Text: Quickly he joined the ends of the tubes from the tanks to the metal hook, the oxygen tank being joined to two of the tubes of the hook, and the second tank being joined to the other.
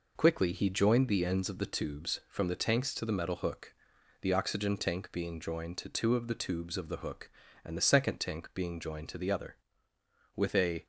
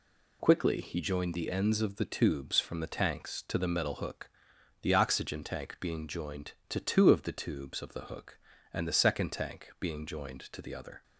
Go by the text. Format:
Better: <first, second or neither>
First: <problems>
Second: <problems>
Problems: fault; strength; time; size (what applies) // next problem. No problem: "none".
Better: second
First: goes on to say "With a"; from 10.3 s on; 0.50 s long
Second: none